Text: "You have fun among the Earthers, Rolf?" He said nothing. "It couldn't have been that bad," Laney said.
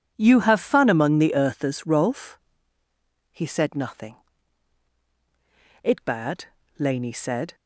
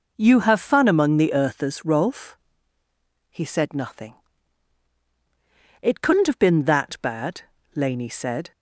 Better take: second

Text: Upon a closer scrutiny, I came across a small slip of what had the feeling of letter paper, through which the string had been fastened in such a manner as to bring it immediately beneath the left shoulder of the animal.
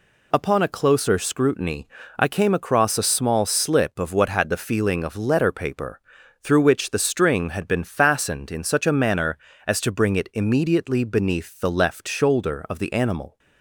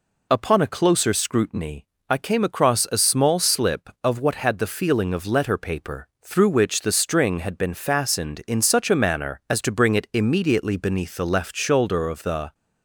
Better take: first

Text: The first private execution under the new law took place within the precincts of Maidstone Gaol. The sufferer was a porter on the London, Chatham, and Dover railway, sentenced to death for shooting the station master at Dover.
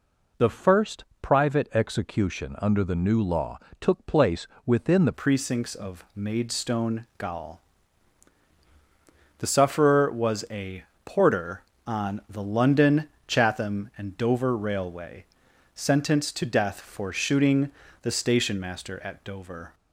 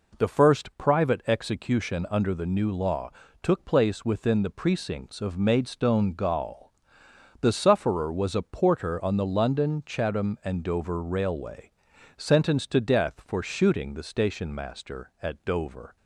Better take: second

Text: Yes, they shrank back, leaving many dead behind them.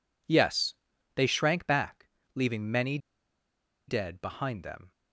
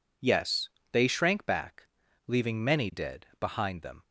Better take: second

